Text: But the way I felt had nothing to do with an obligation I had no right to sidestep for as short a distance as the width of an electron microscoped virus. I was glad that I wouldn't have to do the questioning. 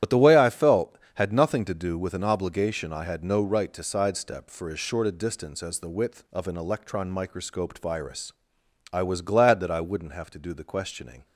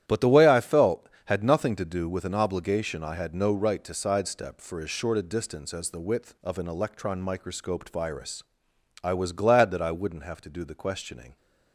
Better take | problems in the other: second | loses the start of "But"; at 0.0 s; 55 ms // starts louder than the rest; strong; until 1.2 s; 11.5 dB; strong in the second

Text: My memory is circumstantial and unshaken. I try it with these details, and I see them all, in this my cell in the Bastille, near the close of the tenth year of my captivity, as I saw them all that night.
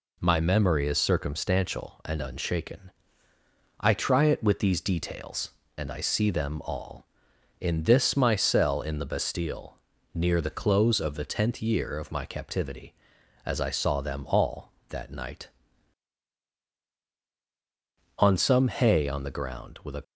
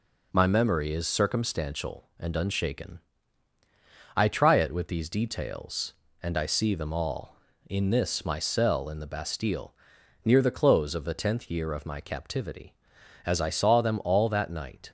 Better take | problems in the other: second | goes on to say "On some hay on the ground with a"; strong; from 18.1 s on; 1.8 s long

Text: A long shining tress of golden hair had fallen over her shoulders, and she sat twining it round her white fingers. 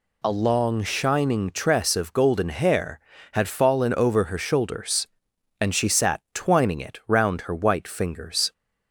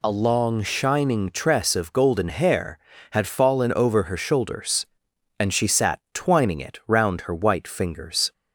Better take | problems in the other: neither | none

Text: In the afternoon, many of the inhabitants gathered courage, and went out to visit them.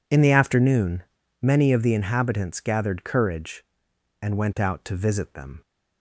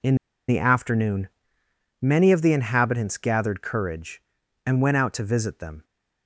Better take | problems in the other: first | pauses between "In" and "the"; slight; at 0.1 s; 0.33 s long

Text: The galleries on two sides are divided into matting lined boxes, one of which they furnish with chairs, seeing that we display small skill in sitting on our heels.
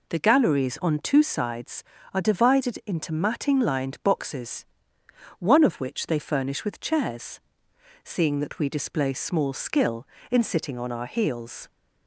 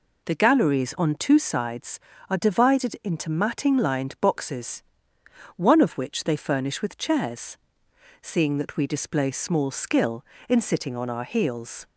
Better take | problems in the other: neither | none

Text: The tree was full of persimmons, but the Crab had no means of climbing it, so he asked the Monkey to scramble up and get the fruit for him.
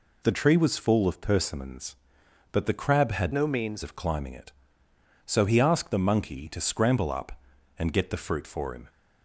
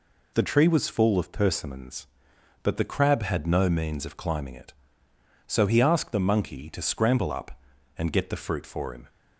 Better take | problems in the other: second | changes voice from "no" to "means"; from 3.3 to 3.8 s; 0.5 s long

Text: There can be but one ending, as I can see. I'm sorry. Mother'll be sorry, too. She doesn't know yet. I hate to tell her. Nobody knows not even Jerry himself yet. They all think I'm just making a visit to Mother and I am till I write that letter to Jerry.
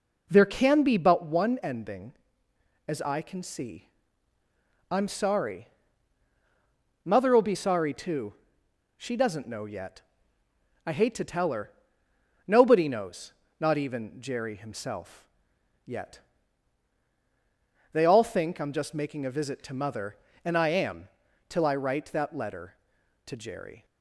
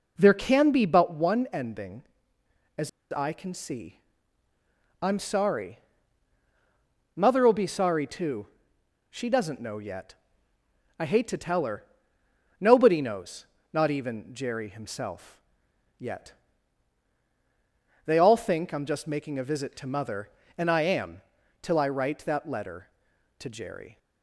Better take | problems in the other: first | pauses between "as" and "I"; slight; at 2.8 s; 0.22 s long // pauses between "knows" and "not"; slight; at 13.4 s; 0.26 s long; slight in the first // pauses between "himself" and "yet"; noticeable; at 15.3 s; 0.58 s long; noticeable in the first // pauses between "am" and "till"; at 21.1 s; 0.42 s long; also in the first

